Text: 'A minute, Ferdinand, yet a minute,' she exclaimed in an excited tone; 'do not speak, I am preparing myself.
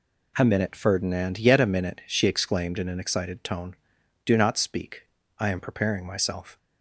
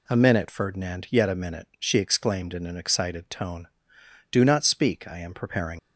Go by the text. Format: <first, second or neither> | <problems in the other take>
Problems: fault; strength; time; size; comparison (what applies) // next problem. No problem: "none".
first | stops before "myself"; at 5.7 s